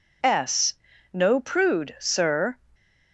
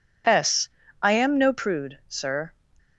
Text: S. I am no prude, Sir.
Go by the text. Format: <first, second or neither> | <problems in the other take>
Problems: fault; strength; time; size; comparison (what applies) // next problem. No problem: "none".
second | skips "I am"; at 0.9 s